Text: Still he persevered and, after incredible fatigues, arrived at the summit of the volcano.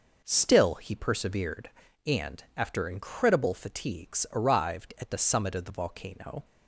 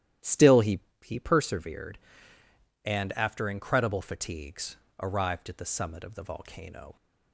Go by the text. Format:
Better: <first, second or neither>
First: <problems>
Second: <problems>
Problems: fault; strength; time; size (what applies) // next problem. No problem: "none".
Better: first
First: none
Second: starts louder than the rest; strong; until 1.4 s; 12 dB // says "he" twice; at 1.0 s